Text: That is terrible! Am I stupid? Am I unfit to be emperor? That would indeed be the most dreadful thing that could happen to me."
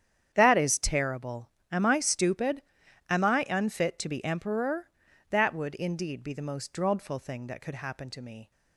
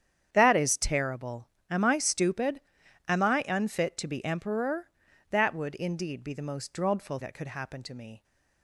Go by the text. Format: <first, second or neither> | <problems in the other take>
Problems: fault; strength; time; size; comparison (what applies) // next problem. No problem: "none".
first | starts louder than the rest; strong; until 1.3 s; 8.5 dB; strong in the first // skips "thing"; at 7.1 s